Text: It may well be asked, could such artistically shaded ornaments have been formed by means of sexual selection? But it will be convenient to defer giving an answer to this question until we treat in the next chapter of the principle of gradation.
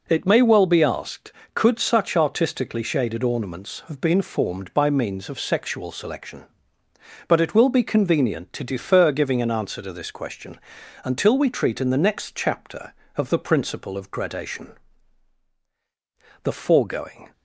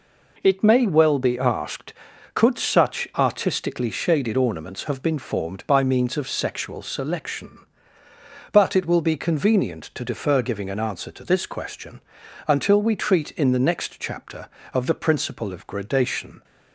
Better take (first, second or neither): second